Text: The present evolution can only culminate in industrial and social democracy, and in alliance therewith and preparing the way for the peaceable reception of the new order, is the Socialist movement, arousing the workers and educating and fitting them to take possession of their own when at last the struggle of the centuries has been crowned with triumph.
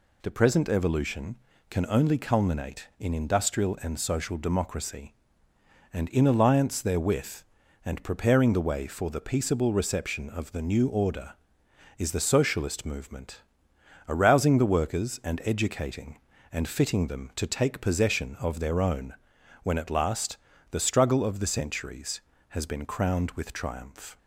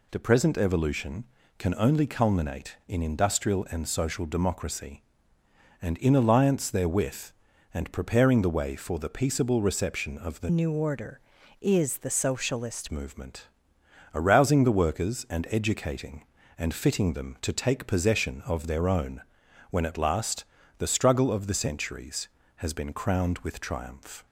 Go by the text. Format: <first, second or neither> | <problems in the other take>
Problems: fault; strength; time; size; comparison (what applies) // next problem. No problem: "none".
first | changes voice from "new" to "Socialist"; from 10.4 to 12.8 s; 2.4 s long // pauses between "own" and "when"; noticeable; at 19.2 s; 0.48 s long; noticeable in the first // pauses between "last" and "the"; slight; at 20.4 s; 0.34 s long; slight in the first